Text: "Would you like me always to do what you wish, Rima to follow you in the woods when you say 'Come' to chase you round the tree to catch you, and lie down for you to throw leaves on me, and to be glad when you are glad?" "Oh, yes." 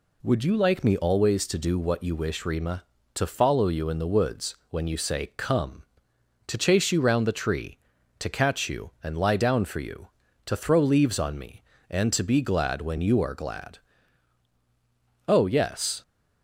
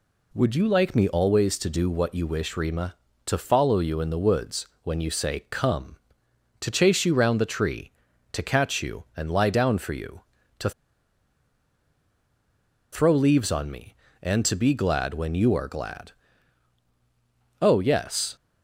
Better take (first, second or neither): first